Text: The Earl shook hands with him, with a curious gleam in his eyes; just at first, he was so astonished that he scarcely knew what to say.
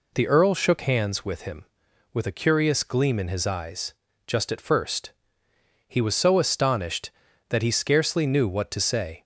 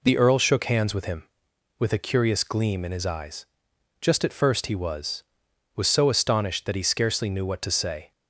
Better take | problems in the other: first | says "was" twice; at 5.7 s

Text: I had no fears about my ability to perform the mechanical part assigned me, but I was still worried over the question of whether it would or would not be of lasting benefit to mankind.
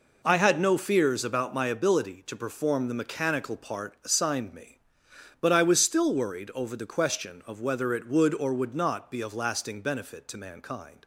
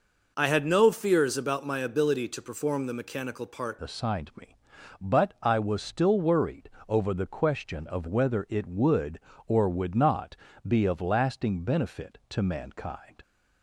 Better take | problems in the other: first | changes voice at "assigned"; from 3.8 s on; 9.3 s long // pauses between "worried" and "over"; slight; at 6.6 s; 0.18 s long // pauses between "not" and "be"; slight; at 10.3 s; 0.28 s long

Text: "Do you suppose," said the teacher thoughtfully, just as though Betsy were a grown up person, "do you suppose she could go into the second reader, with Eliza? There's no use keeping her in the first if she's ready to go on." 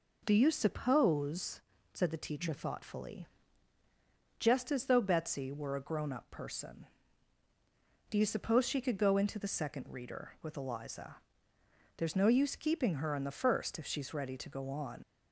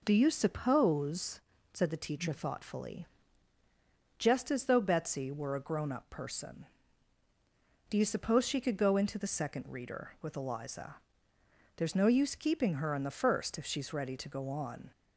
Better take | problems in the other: second | leaves "on" unfinished; at 15.0 s; 90 ms

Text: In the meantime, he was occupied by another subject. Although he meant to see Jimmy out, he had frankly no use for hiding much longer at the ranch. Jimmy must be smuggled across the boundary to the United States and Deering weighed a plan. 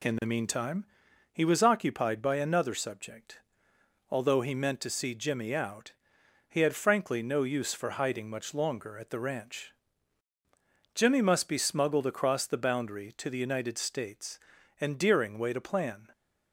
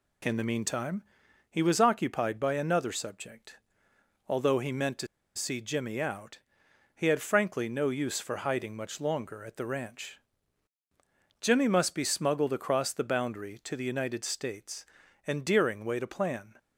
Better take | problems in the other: first | pauses between "to" and "see"; slight; at 5.0 s; 0.29 s long

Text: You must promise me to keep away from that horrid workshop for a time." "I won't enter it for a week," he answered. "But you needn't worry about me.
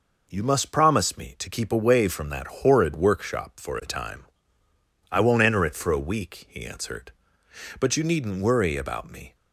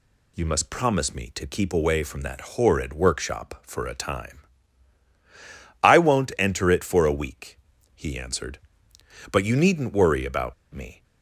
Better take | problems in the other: first | pauses between "about" and "me"; slight; at 10.5 s; 0.18 s long

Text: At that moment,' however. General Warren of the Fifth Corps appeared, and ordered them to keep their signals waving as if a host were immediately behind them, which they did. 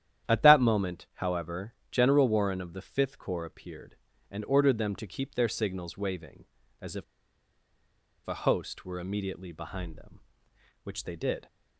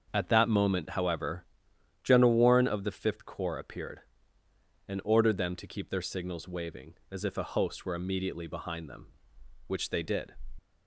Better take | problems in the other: second | starts louder than the rest; strong; until 1.3 s; 10.5 dB; also in the second // pauses between "if" and "a"; at 7.0 s; 1.2 s long

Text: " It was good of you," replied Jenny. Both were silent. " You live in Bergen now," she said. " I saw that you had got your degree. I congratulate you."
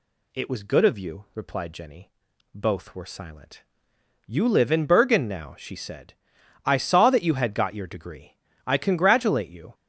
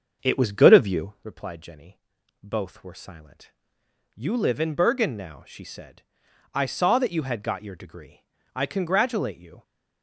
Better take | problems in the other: first | starts louder than the rest; until 1.2 s; 7 dB

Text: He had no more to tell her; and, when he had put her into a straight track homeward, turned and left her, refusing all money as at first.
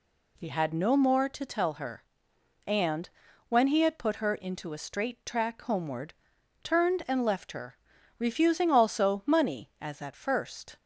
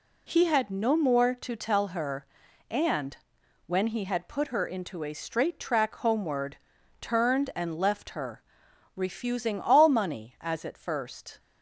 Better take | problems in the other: second | says "also" for "all"; at 8.7 s

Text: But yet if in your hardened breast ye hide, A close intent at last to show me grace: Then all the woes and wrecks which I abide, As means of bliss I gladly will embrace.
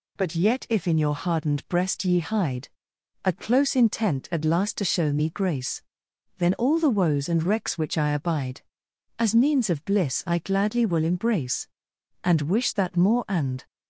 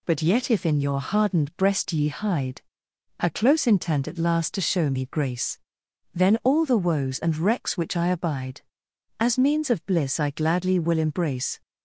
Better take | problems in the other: second | goes on to say "And wish that more and"; from 12.2 s on; 1.4 s long

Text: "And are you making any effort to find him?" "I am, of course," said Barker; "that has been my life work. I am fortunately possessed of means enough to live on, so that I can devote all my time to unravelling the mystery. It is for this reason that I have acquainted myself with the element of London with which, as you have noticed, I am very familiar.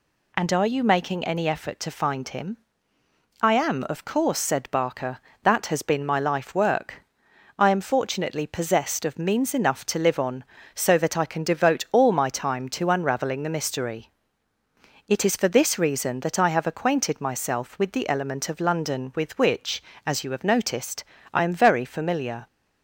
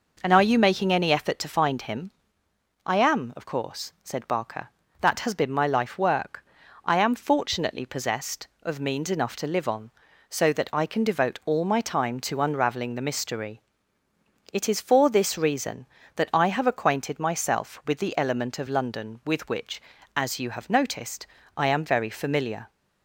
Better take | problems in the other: neither | none

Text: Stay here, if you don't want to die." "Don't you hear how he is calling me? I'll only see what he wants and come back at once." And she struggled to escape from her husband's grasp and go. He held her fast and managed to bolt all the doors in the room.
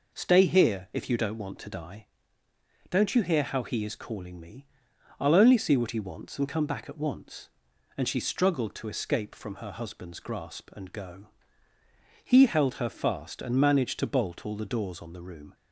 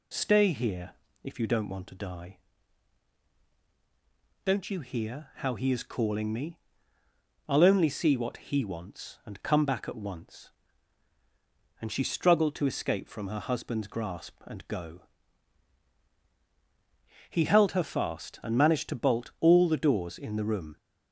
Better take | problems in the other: second | says "on" for "in"; at 15.0 s

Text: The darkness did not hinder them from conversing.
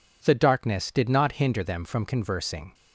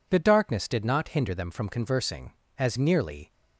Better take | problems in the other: first | goes on to say "As nearly"; noticeable; from 2.5 s on; 0.76 s long

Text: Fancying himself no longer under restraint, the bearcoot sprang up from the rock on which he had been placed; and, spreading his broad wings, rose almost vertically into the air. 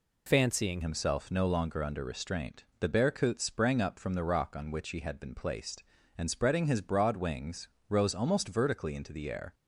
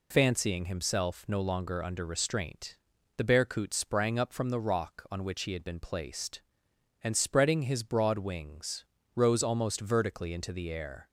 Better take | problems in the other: second | changes voice at "himself"; from 0.8 s on; 8.7 s long

